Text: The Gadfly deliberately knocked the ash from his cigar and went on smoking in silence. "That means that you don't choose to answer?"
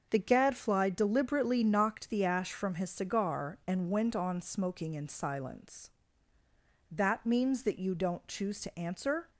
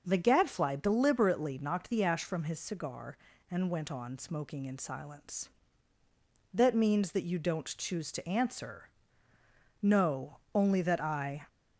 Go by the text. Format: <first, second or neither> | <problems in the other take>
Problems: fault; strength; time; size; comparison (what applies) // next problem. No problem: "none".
first | starts louder than the rest; until 1.0 s; 6.5 dB; also in the first // goes on to say "No only that I"; from 9.8 s on; 1.6 s long